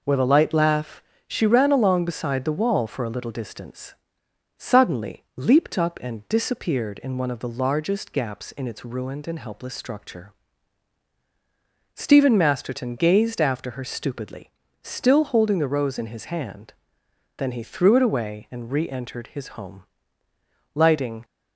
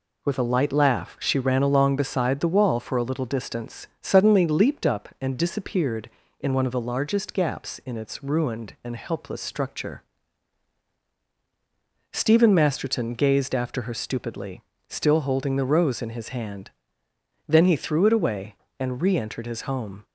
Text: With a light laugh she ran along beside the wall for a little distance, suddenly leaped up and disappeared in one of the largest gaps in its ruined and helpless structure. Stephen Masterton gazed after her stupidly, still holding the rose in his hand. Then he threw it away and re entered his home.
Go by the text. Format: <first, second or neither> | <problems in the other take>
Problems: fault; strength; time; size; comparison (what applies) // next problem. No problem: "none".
second | pauses between "laugh" and "she"; slight; at 1.0 s; 0.24 s long // goes on to say "Lighting"; from 20.7 s on; 0.50 s long